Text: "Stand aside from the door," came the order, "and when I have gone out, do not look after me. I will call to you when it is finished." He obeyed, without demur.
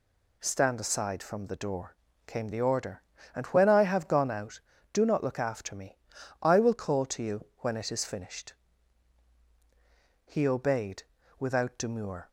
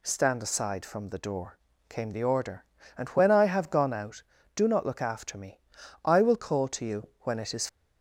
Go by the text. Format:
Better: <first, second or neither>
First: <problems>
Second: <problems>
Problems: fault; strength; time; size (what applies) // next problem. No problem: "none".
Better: first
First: none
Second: stops before "finished He obeyed without demur"; at 7.6 s